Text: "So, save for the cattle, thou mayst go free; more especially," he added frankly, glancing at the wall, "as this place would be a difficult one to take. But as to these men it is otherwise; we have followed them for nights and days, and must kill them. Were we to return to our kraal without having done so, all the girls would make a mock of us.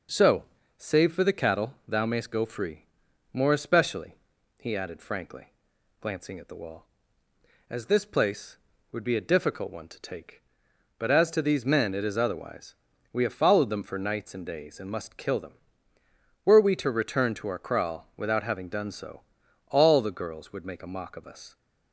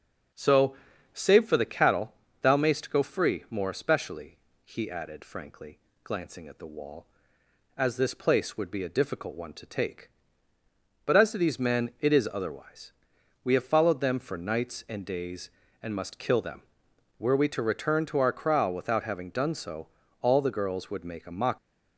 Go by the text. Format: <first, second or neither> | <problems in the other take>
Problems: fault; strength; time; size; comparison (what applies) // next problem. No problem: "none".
first | starts louder than the rest; until 1.7 s; 6.5 dB // stops before "of us"; at 21.5 s